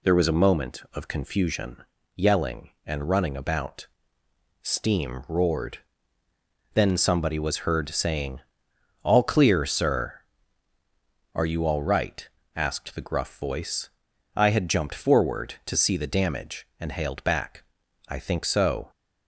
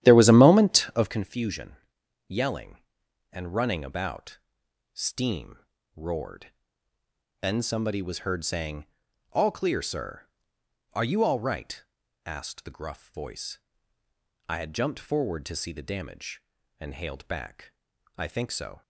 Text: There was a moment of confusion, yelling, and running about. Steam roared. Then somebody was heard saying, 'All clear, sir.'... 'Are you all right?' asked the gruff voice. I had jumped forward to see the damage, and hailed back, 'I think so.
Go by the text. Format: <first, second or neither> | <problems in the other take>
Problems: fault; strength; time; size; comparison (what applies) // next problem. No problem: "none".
first | starts louder than the rest; strong; until 1.2 s; 12 dB // pauses between "Steam" and "roared"; at 5.5 s; 0.38 s long